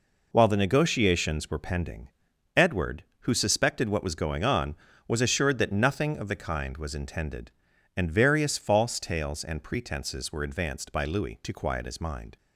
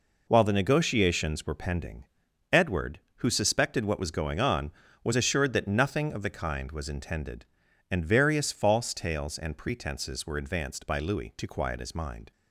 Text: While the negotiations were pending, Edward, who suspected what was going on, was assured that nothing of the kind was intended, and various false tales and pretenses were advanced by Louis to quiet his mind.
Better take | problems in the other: neither | none

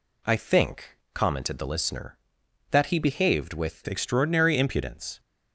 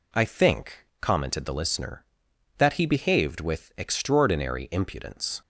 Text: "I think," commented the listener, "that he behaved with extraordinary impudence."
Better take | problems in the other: second | changes voice at "extraordinary"; from 3.8 s on; 1.3 s long

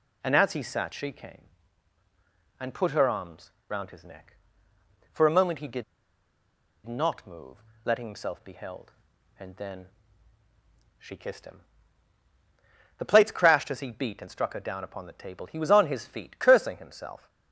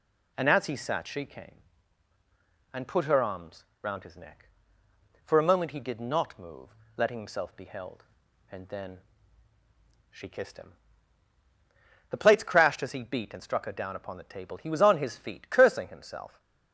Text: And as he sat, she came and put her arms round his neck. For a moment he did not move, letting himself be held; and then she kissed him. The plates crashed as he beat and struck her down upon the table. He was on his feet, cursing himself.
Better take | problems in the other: second | pauses between "arms" and "round"; slight; at 3.5 s; 0.18 s long; slight in the second // pauses between "did" and "not"; at 5.8 s; 1.0 s long // pauses between "then" and "she"; at 9.8 s; 1.1 s long; also in the second

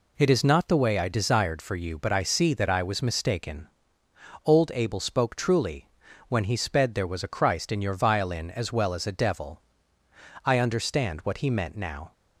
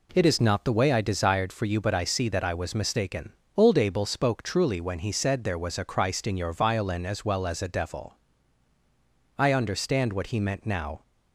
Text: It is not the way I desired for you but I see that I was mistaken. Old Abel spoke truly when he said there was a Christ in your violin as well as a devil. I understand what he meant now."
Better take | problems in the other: second | pauses between "truly" and "when"; at 5.8 s; 0.40 s long // says "sped" for "said"; at 6.5 s

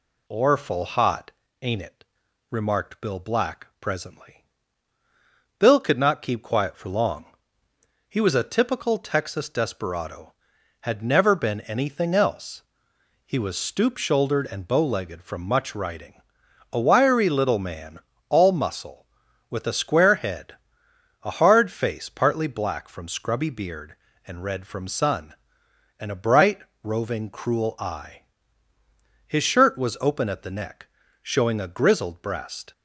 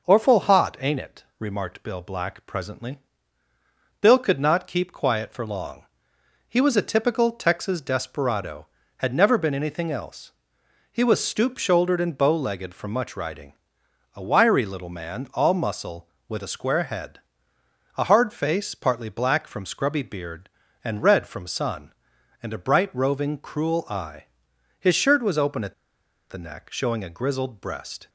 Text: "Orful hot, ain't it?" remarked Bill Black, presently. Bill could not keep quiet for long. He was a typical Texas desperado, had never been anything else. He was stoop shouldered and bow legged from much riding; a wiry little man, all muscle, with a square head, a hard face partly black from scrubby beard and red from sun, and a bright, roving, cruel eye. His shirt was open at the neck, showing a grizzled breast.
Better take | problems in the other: first | pauses between "at" and "the"; noticeable; at 25.7 s; 0.57 s long

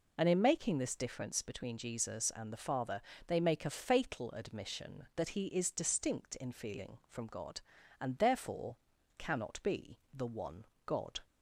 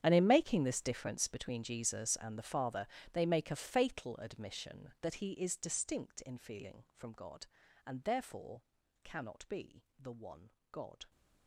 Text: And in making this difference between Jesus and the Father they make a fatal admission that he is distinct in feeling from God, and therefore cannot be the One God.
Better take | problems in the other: first | gets quieter; strong; throughout; 19 dB // pauses between "Father" and "they"; slight; at 2.8 s; 0.26 s long; slight in the first // pauses between "therefore" and "cannot"; at 8.6 s; 0.42 s long; also in the first // pauses between "be" and "the"; slight; at 9.8 s; 0.16 s long; slight in the first // pauses between "One" and "God"; slight; at 10.5 s; 0.20 s long; slight in the first

